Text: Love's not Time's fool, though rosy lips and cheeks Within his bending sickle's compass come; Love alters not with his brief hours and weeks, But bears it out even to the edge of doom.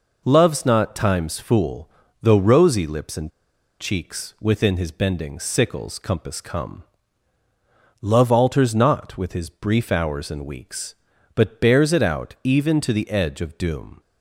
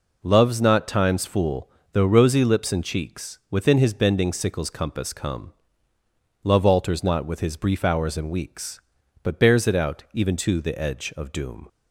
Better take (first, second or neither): second